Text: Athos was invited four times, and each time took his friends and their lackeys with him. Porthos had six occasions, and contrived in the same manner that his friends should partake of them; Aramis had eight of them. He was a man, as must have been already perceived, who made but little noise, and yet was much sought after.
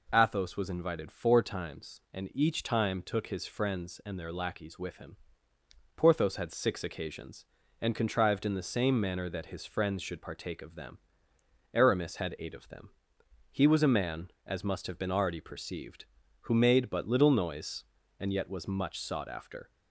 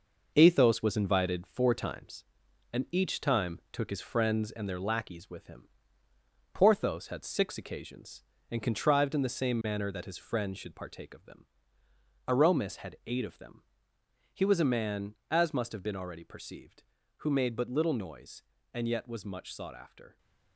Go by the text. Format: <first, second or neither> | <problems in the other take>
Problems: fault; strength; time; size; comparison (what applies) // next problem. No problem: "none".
first | gets quieter; throughout; 6.5 dB